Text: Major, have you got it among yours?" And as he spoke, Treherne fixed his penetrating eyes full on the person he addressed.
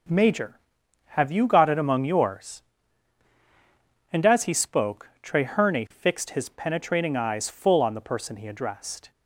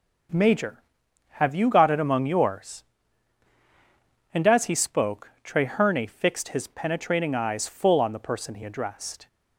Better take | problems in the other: neither | none

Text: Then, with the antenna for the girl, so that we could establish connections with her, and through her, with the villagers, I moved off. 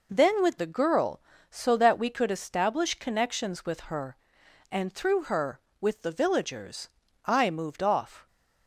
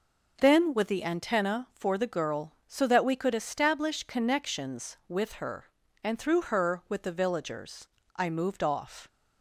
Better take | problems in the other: second | skips "the antenna for"; at 0.5 s

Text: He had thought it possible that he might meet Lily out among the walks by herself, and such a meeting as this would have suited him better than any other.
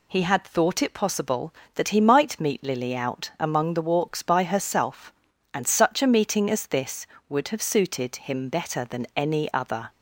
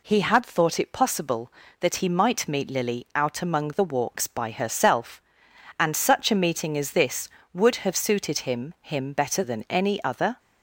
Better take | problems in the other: first | says "him" twice; at 8.8 s

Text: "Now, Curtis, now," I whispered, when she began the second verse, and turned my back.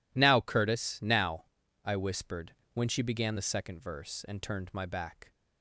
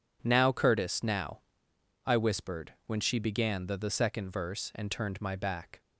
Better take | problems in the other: first | says "the" twice; at 3.7 s

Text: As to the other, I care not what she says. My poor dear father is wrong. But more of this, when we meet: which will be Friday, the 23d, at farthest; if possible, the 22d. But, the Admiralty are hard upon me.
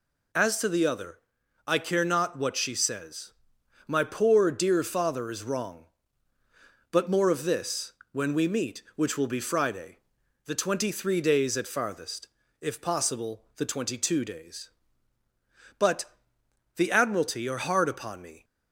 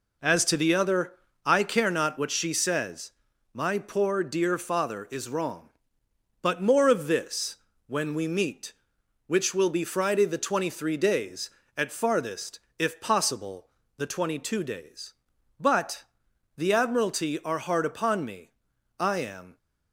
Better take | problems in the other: first | goes on to say "I am"; from 18.9 s on; 0.58 s long

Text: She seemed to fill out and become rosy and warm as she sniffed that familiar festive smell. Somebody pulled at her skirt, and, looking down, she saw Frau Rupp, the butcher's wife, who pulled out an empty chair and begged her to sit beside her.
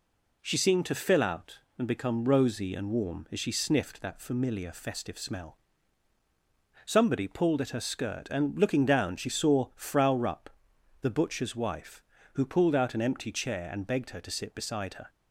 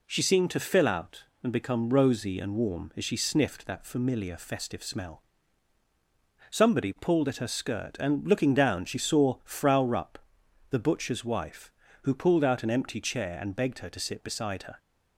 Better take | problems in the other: neither | none

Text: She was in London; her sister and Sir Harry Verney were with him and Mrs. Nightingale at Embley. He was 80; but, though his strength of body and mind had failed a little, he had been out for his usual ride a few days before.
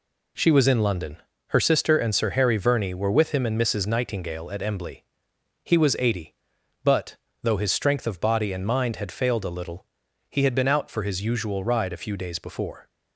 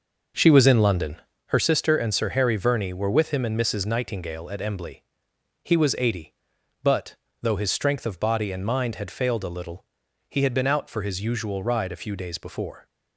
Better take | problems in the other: first | starts louder than the rest; noticeable; until 1.5 s; 6 dB

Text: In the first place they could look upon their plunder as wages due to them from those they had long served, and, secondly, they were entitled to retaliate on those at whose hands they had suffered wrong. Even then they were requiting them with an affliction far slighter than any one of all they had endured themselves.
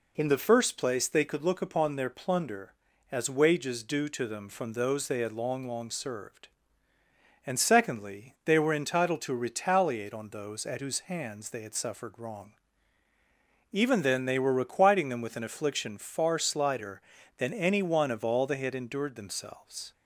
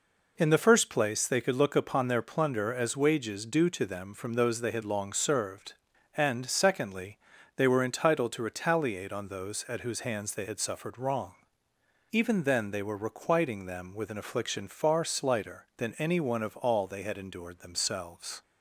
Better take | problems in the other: second | says "long" twice; at 5.6 s

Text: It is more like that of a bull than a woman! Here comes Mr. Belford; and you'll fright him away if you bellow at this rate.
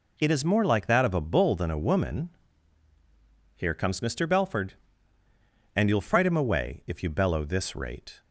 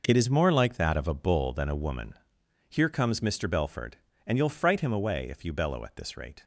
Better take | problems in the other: second | skips "at"; at 7.4 s

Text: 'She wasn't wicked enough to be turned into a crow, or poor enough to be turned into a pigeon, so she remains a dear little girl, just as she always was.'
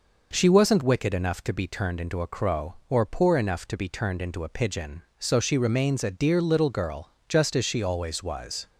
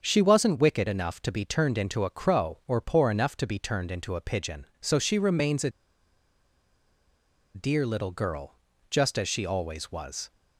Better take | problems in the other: first | starts louder than the rest; until 1.0 s; 6.5 dB // pauses between "a" and "dear"; strong; at 5.6 s; 1.8 s long

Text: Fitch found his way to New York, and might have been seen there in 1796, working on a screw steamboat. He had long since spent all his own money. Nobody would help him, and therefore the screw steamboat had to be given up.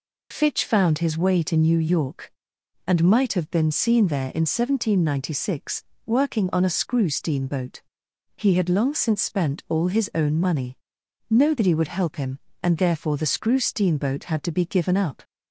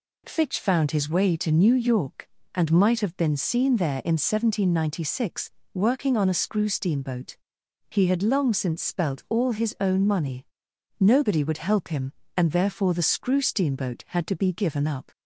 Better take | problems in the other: first | says "spelt" for "spent"; at 8.8 s

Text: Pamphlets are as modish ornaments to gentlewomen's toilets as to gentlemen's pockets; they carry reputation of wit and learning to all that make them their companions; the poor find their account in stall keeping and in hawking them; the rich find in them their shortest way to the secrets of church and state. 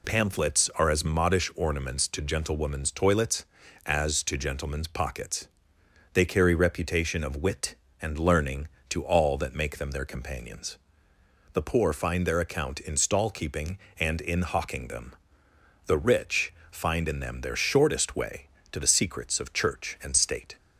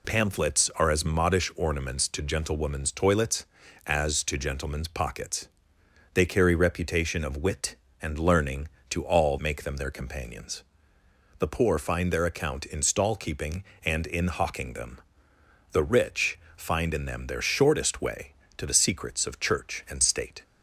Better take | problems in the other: first | skips "that"; at 9.3 s // pauses between "rich" and "find"; slight; at 16.3 s; 0.16 s long; slight in the first

